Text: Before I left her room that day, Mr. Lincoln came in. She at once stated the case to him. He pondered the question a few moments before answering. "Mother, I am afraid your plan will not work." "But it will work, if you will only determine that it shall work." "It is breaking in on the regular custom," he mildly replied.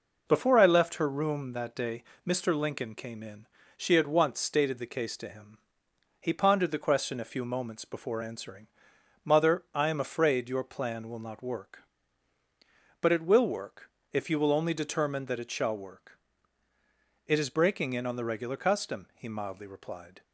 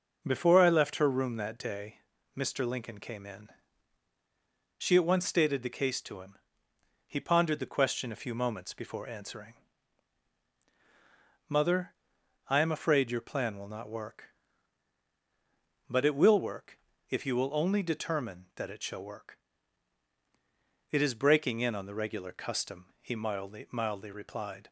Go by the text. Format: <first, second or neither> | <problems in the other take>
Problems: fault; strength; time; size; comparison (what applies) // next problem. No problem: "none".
first | says "mildly" twice; at 23.7 s